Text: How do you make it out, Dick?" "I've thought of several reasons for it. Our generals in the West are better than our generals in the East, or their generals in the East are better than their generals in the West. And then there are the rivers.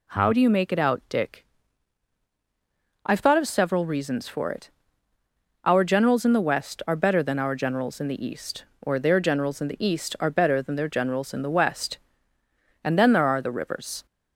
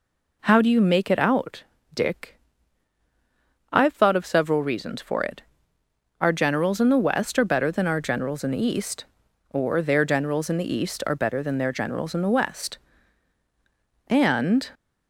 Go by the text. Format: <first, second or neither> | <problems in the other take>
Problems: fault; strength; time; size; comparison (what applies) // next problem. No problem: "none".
first | stops before "then there are the rivers"; at 14.7 s